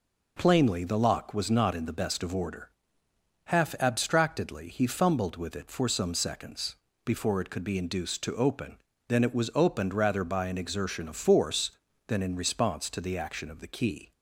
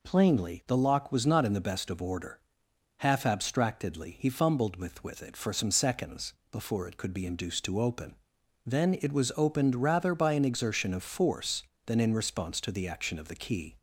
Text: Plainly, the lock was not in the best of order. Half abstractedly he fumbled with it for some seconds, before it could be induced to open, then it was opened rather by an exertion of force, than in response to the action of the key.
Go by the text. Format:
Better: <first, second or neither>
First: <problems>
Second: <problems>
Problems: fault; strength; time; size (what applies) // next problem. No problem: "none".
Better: first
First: none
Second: says "with" twice; at 5.0 s